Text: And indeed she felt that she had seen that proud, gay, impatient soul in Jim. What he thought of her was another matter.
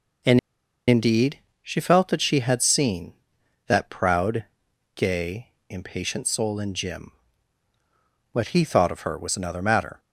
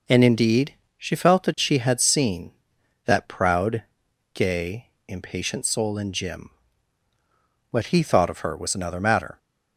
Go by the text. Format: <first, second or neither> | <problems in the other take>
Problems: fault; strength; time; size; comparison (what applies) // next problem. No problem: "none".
second | pauses between "And" and "indeed"; noticeable; at 0.3 s; 0.48 s long // pauses between "indeed" and "she"; slight; at 1.3 s; 0.22 s long; slight in the second